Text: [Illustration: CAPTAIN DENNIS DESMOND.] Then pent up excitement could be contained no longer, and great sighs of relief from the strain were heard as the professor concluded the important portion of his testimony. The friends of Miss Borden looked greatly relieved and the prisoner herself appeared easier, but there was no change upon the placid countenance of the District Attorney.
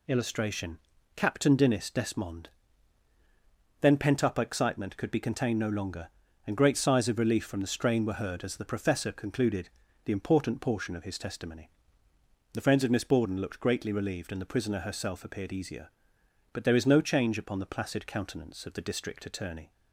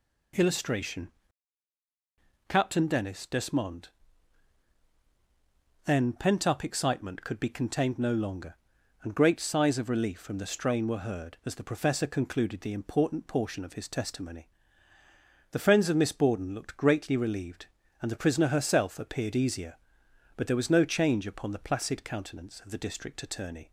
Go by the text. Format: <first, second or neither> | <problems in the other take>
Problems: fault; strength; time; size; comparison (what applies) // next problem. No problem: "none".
second | pauses between "concluded" and "the"; slight; at 9.6 s; 0.34 s long // says "is" for "was"; at 16.7 s